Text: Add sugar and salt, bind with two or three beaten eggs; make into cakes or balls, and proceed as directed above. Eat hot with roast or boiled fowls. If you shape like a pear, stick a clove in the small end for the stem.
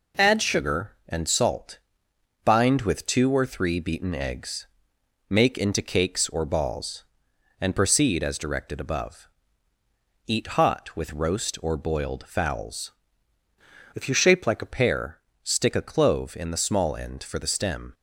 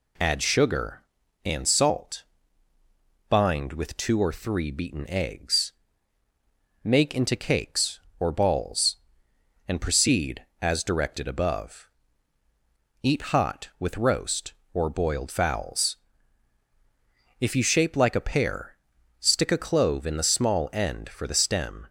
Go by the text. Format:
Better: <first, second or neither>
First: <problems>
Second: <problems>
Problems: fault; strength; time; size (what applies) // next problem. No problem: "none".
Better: second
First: changes voice from "If" to "a"; from 13.9 to 14.7 s; 0.8 s long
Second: none